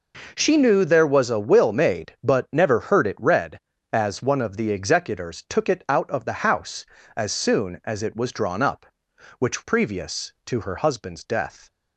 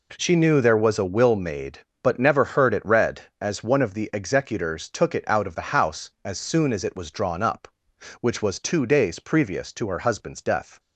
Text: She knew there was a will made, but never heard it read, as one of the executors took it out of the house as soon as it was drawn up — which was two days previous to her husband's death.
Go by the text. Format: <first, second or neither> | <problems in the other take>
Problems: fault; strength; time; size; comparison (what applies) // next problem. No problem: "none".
second | skips "was two days"; at 9.6 s